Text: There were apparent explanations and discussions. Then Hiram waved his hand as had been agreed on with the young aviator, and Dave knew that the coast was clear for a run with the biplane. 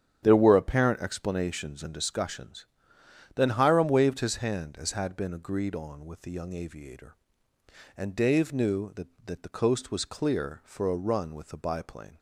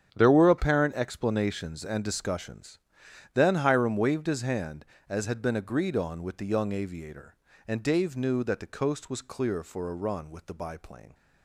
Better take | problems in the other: second | starts louder than the rest; strong; until 1.2 s; 9 dB; strong in the second // says "that" twice; at 9.2 s

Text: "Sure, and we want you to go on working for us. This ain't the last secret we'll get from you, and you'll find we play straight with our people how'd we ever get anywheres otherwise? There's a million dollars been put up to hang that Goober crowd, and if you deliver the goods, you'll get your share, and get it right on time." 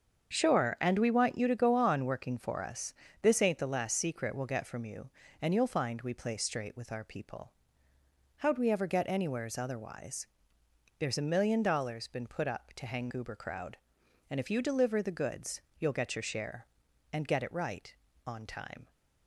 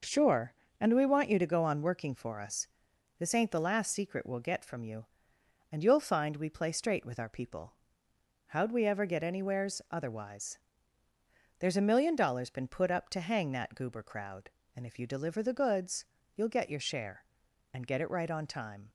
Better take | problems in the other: second | starts louder than the rest; until 1.3 s; 7 dB // pauses between "people" and "how'd"; noticeable; at 7.5 s; 0.86 s long; noticeable in the second // skips "that"; at 13.0 s

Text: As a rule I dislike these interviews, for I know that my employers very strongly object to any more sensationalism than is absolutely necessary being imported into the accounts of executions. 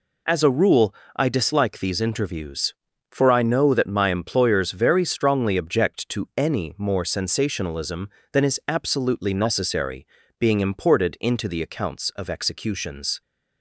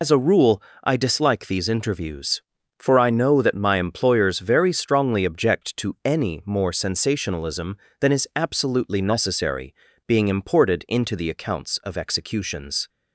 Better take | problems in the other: first | loses the start of "As"; at 0.0 s; 75 ms // pauses between "rule" and "I"; slight; at 0.6 s; 0.22 s long; slight in the first // pauses between "necessary" and "being"; slight; at 9.7 s; 0.34 s long; slight in the first

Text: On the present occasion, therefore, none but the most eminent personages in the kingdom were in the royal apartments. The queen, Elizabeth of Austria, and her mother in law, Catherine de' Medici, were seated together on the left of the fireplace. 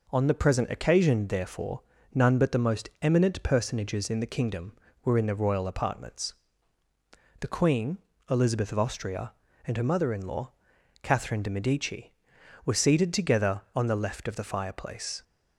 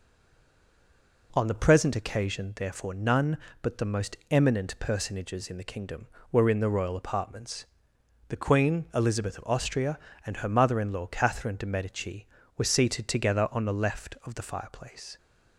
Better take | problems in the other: first | stays silent before the first word; noticeable; until 1.3 s; 1.3 s long

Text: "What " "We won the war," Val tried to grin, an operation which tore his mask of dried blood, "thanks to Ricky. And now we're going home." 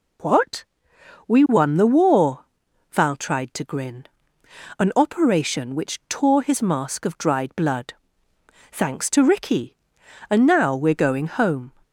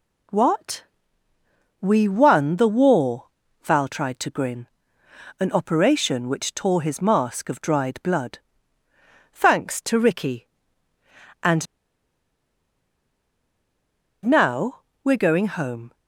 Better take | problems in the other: first | pauses between "And" and "now"; strong; at 11.6 s; 2.6 s long // pauses between "now" and "we're"; slight; at 14.8 s; 0.20 s long

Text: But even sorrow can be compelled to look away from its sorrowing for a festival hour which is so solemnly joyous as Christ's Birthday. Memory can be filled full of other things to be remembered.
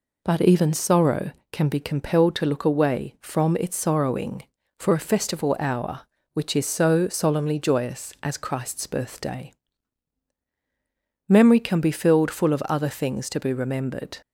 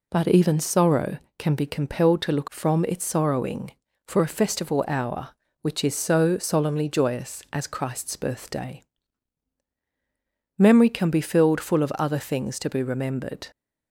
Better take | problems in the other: first | skips "away"; at 2.4 s

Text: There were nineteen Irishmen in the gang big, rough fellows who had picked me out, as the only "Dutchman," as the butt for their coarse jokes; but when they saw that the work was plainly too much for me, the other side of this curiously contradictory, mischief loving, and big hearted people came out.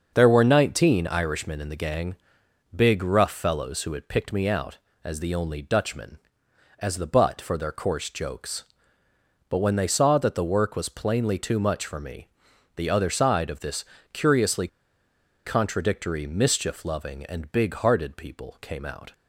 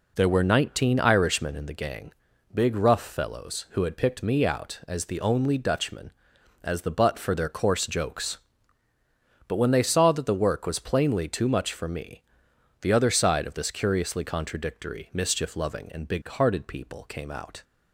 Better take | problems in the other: second | starts louder than the rest; until 1.1 s; 6.5 dB // pauses between "gang" and "big"; noticeable; at 2.1 s; 0.60 s long; also in the second // pauses between "this" and "curiously"; slight; at 13.8 s; 0.28 s long // pauses between "curiously" and "contradictory"; noticeable; at 14.6 s; 0.78 s long

